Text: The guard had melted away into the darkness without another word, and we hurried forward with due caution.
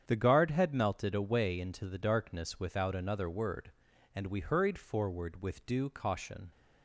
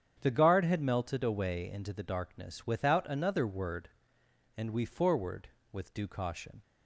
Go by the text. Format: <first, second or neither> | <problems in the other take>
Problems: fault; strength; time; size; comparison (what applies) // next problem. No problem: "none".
first | starts louder than the rest; strong; until 1.2 s; 8.5 dB; strong in the first // skips "hurried"; at 4.8 s